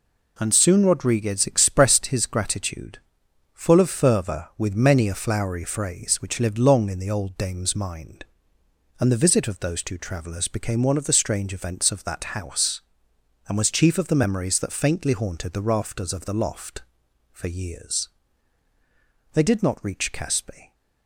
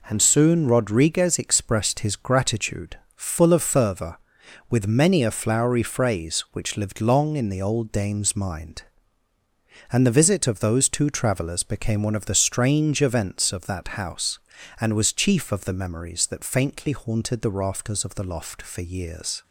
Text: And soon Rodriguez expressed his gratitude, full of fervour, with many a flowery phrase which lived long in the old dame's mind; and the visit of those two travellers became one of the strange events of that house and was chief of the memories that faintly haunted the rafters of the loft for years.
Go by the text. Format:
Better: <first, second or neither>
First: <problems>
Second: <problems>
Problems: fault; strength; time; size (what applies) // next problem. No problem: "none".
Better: second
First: goes on to say "They did not reach Caspe"; from 19.3 s on; 1.4 s long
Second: none